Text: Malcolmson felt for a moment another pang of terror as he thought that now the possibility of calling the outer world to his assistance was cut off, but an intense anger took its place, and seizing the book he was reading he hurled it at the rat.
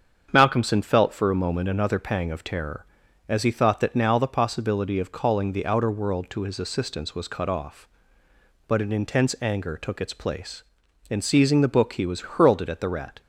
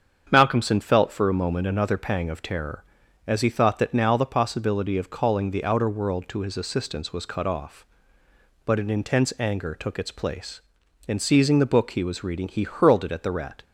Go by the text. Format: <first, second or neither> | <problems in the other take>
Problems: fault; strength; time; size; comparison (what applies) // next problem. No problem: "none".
second | starts louder than the rest; strong; until 1.3 s; 7.5 dB; strong in the second // skips "reading he"; at 12.2 s